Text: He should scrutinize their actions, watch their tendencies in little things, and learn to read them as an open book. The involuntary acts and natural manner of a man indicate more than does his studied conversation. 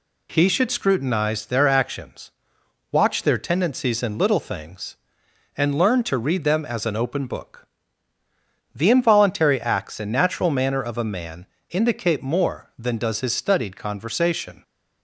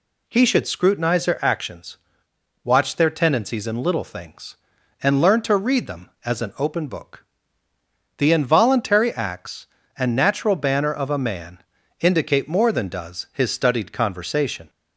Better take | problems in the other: first | says "banner" for "manner"; at 10.5 s // pauses between "man" and "indicate"; at 11.5 s; 0.42 s long; slight in the first

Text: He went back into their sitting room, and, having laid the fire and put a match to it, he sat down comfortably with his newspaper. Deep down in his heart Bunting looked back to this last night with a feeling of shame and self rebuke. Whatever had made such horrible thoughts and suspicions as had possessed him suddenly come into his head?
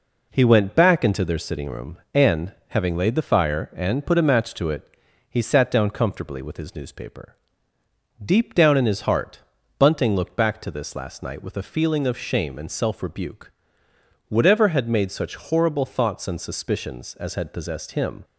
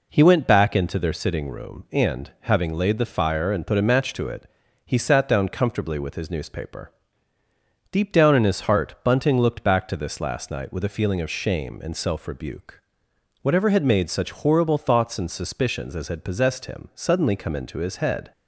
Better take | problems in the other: second | pauses between "heart" and "Bunting"; at 9.4 s; 0.38 s long // stops before "suddenly come into his head"; at 18.2 s

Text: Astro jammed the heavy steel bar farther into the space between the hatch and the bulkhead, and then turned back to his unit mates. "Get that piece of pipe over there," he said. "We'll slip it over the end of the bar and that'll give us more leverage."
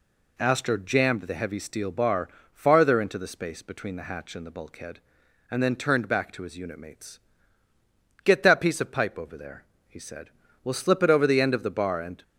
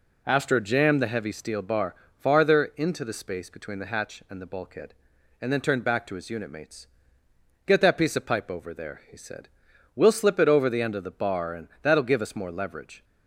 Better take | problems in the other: second | pauses between "bar" and "farther"; slight; at 2.2 s; 0.24 s long; slight in the second // stops before "that'll give us more leverage"; at 12.2 s

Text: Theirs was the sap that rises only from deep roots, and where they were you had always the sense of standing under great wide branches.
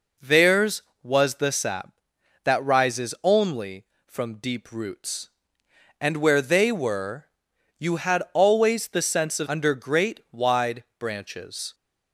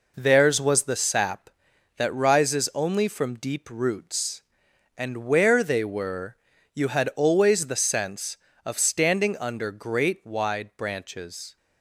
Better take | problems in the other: second | pauses between "were" and "you"; noticeable; at 7.2 s; 0.50 s long; slight in the second // skips "standing"; at 9.4 s

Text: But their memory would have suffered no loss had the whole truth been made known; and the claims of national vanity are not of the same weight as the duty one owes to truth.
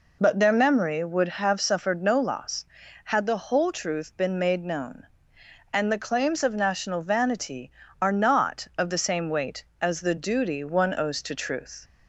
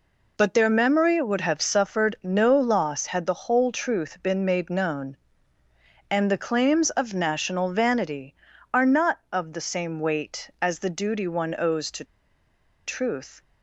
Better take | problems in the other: first | pauses between "to" and "truth"; noticeable; at 12.0 s; 0.82 s long

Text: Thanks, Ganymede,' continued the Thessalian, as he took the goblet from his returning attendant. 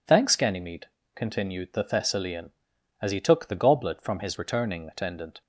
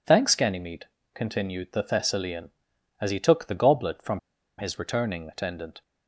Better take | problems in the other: first | pauses between "from" and "his"; at 4.1 s; 0.40 s long

